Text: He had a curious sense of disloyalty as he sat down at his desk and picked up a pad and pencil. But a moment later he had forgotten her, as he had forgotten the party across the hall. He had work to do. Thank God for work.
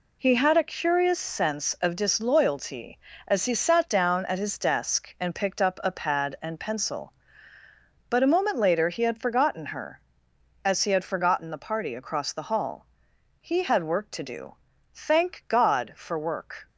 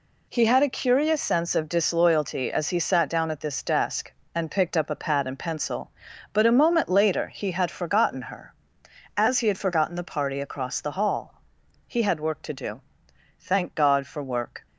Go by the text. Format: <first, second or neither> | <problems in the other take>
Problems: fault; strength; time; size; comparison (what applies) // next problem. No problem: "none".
first | says "this" for "his"; at 3.4 s